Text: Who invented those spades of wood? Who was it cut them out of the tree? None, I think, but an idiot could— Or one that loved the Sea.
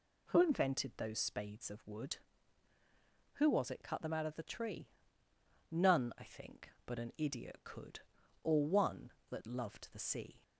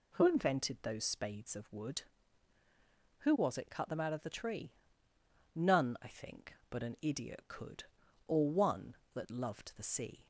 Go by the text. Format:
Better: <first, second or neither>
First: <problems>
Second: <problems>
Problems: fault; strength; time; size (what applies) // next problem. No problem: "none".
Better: neither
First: none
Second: none